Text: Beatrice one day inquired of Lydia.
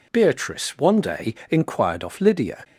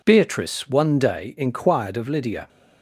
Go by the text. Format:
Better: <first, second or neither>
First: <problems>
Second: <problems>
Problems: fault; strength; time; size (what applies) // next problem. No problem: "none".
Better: second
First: pauses between "day" and "inquired"; slight; at 1.3 s; 0.16 s long // says "off" for "of"; at 2.0 s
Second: none